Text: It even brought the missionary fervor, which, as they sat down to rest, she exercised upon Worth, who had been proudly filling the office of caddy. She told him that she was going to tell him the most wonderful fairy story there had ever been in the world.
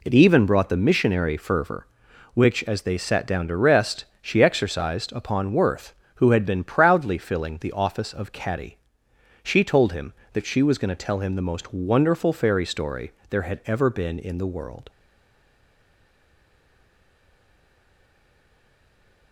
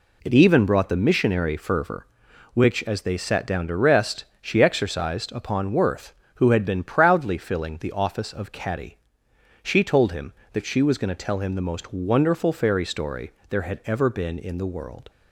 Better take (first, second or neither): second